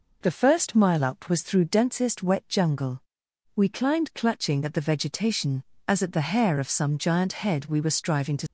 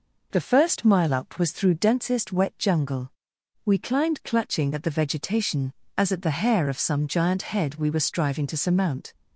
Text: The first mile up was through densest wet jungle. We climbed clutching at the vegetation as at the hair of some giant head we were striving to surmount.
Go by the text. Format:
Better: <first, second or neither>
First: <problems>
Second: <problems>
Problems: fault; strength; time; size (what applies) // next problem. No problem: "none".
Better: second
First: stops before "surmount"; at 8.4 s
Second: none